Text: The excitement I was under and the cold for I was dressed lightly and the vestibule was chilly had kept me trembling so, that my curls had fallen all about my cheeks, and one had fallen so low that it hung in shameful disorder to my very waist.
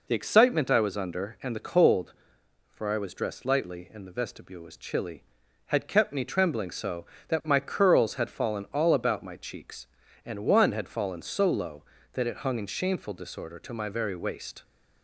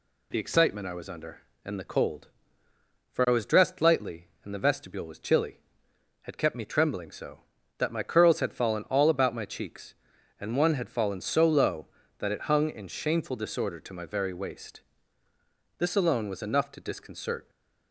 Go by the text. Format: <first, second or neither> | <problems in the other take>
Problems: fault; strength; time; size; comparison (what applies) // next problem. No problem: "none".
first | goes on to say "This alone was enough to disconcert"; strong; from 15.7 s on; 1.7 s long